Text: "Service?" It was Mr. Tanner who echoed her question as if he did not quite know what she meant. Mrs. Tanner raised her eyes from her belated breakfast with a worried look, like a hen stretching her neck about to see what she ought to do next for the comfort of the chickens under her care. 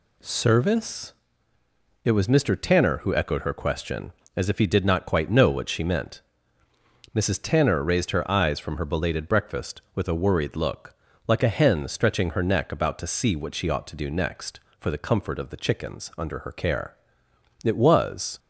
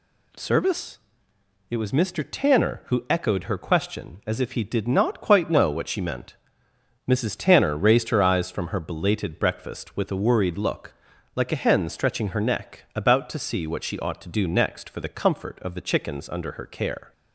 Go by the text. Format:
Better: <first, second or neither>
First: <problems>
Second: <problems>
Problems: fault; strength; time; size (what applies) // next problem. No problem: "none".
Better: second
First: goes on to say "It was"; noticeable; from 17.6 s on; 0.74 s long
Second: none